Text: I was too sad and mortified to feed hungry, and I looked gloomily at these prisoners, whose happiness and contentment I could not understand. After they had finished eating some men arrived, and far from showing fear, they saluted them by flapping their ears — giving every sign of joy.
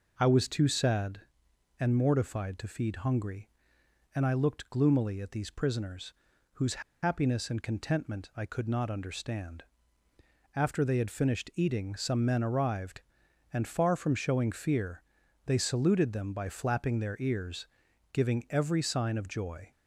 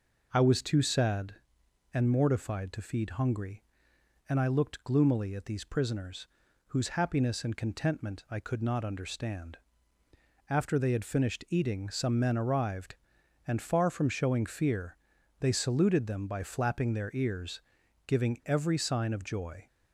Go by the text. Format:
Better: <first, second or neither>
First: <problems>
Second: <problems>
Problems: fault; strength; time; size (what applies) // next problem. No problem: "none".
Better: second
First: pauses between "whose" and "happiness"; slight; at 6.8 s; 0.21 s long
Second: none